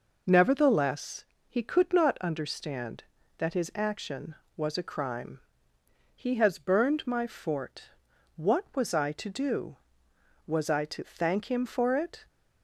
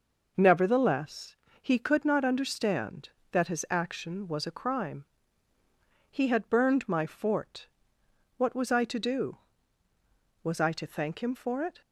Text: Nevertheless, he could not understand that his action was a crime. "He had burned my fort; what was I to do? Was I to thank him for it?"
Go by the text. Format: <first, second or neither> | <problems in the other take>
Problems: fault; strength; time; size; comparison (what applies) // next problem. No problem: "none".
second | says "has" for "had"; at 6.3 s